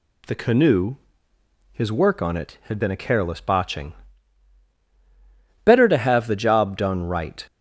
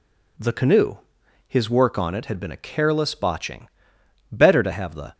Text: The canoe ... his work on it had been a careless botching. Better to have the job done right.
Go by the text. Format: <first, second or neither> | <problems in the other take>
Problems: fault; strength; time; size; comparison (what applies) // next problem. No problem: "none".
first | stops before "job done right"; at 5.1 s